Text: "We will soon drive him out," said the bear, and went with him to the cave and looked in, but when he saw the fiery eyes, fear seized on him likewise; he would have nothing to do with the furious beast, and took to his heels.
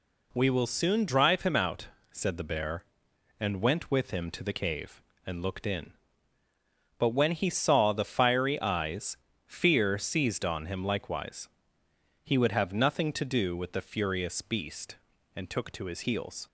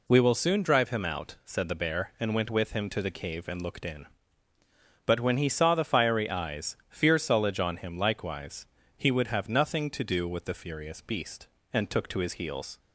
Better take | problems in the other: first | says "sullage" for "seized"; at 7.1 s

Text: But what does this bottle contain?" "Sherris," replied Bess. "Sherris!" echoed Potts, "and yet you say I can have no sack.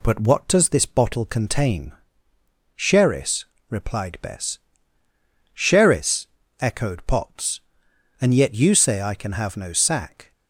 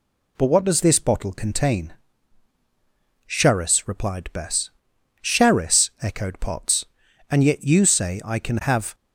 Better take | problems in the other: first | stops before "no sack"; at 8.9 s

